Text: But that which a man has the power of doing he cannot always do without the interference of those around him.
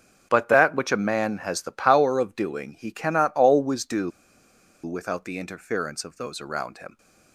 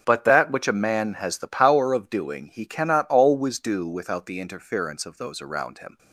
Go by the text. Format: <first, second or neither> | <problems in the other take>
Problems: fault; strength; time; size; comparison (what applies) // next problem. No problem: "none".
second | starts louder than the rest; until 1.3 s; 6.5 dB; also in the second // pauses between "do" and "without"; noticeable; at 4.1 s; 0.74 s long